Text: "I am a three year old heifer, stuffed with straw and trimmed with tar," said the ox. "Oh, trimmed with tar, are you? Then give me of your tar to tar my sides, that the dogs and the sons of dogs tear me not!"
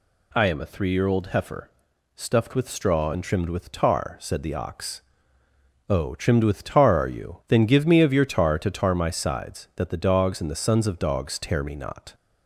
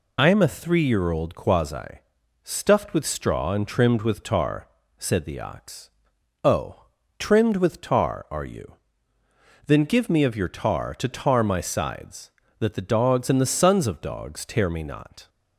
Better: first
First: none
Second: says "quasi" for "heifer"; at 1.3 s

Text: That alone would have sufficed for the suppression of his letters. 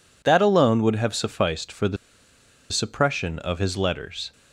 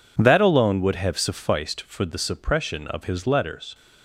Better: second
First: pauses between "the" and "suppression"; noticeable; at 1.9 s; 0.75 s long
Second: none

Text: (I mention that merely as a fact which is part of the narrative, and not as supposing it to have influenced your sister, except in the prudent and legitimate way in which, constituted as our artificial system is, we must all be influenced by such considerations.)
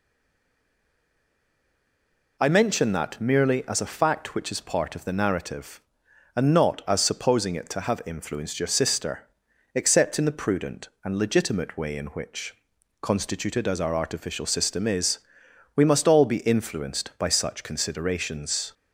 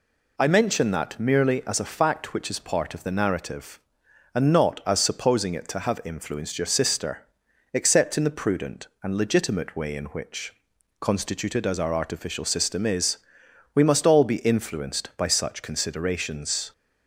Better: second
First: stays silent before the first word; until 2.3 s; 2.3 s long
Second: none

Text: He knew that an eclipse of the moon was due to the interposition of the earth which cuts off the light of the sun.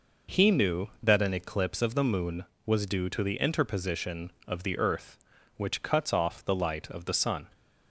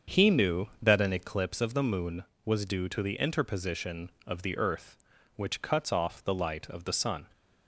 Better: first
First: none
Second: starts louder than the rest; until 1.4 s; 7 dB

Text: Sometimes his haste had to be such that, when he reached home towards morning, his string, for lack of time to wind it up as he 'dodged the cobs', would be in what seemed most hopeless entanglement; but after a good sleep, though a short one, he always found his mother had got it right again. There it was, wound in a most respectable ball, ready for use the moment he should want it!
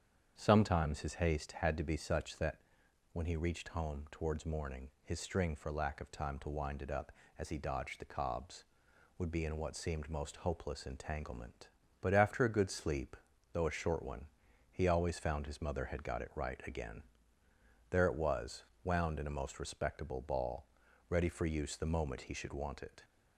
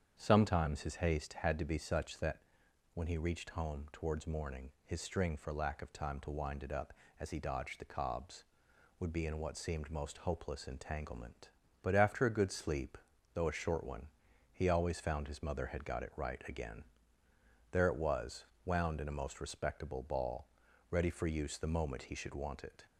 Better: neither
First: starts louder than the rest; strong; until 1.3 s; 8 dB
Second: starts louder than the rest; strong; until 1.1 s; 8 dB

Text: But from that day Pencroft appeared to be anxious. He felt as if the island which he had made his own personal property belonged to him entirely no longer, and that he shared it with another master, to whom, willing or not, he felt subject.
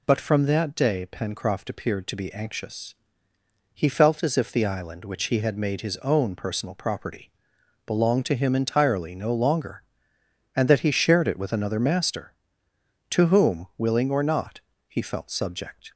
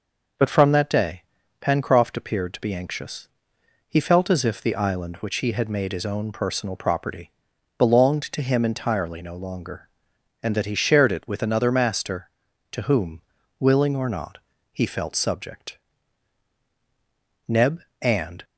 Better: first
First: pauses between "property" and "belonged"; noticeable; at 7.3 s; 0.54 s long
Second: pauses between "day" and "Pencroft"; at 1.2 s; 0.38 s long // pauses between "property" and "belonged"; noticeable; at 7.2 s; 0.48 s long // goes on to say "Neb and"; noticeable; from 17.4 s on; 0.96 s long

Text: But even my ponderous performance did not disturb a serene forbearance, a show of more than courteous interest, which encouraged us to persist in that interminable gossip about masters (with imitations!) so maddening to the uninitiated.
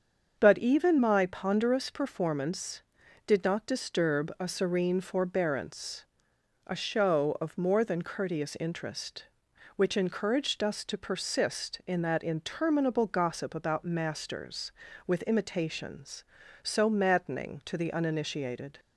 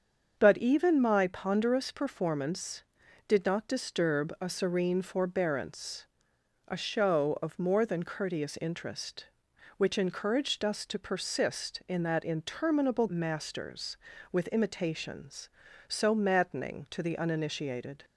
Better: first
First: starts louder than the rest; until 1.3 s; 7 dB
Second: starts louder than the rest; until 1.3 s; 7 dB // skips "gossip about"; at 13.0 s

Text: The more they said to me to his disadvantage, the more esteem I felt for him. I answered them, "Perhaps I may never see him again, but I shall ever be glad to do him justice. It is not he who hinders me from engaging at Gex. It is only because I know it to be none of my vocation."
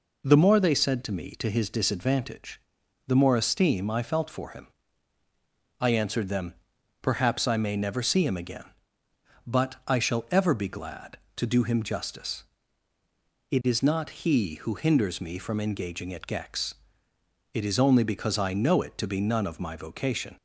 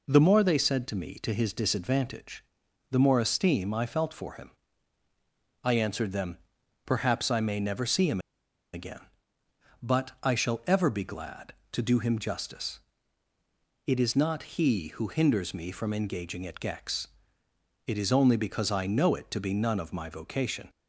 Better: first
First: none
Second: pauses between "him" and "again"; noticeable; at 8.1 s; 0.54 s long

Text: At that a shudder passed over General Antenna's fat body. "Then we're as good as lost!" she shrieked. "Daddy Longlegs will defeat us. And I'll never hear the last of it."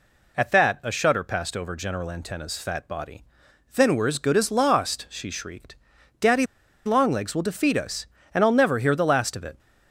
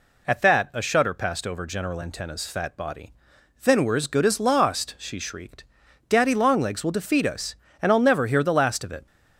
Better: second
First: pauses between "Daddy" and "Longlegs"; at 6.4 s; 0.40 s long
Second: none

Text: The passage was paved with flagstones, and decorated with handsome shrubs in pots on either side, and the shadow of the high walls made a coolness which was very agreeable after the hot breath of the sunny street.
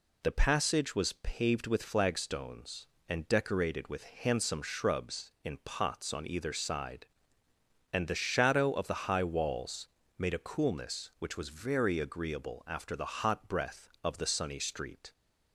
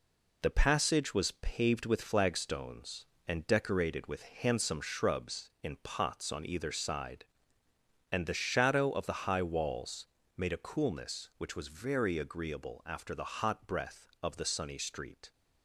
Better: first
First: pauses between "walls" and "made"; slight; at 9.8 s; 0.30 s long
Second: gets quieter; noticeable; throughout; 5.5 dB // pauses between "walls" and "made"; slight; at 10.0 s; 0.30 s long

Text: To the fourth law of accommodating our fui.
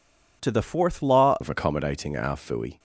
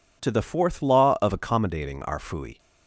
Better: second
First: changes voice at "of"; from 1.4 s on; 1.3 s long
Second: none

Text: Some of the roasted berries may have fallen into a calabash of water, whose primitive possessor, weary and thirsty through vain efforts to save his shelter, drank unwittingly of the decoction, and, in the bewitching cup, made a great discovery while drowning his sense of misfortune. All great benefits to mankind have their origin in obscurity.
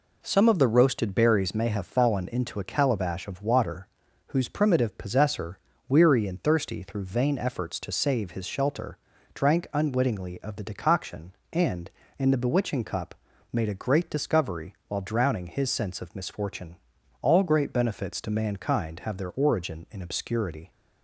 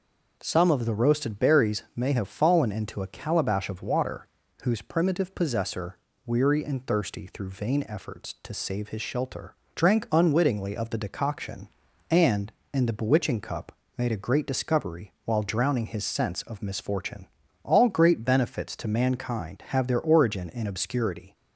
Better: neither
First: none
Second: none

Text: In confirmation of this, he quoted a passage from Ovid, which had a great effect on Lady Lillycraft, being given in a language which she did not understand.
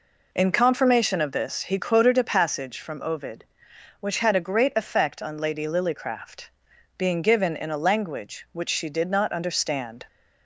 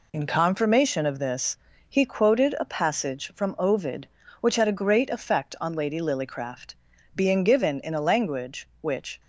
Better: first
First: none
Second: stops before "she did not understand"; at 9.1 s

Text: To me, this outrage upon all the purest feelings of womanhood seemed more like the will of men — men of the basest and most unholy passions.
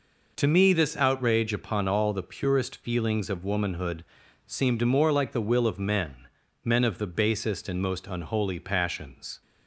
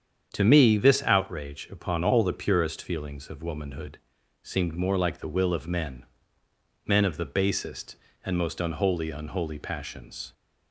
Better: first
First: pauses between "womanhood" and "seemed"; at 4.0 s; 0.42 s long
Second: starts louder than the rest; strong; until 1.3 s; 8 dB // pauses between "womanhood" and "seemed"; noticeable; at 3.9 s; 0.46 s long // says "unholy" twice; at 9.0 s

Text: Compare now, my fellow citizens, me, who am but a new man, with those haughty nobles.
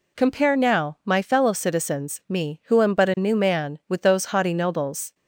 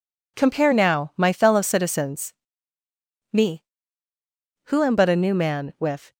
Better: first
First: none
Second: stops before "those haughty nobles"; at 6.1 s

